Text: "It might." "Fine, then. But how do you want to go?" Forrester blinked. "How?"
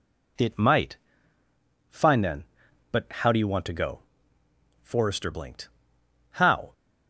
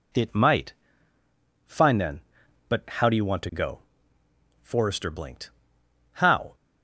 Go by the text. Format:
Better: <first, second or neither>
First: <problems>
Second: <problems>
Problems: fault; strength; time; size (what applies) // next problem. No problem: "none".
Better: neither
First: none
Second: none